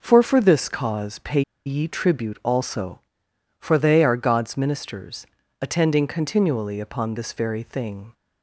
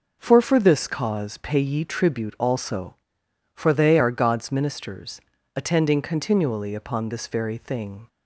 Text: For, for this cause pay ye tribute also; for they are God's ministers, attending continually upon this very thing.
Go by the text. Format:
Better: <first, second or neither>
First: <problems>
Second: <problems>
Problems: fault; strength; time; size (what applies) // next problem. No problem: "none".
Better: second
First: pauses between "pay" and "ye"; slight; at 1.4 s; 0.24 s long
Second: none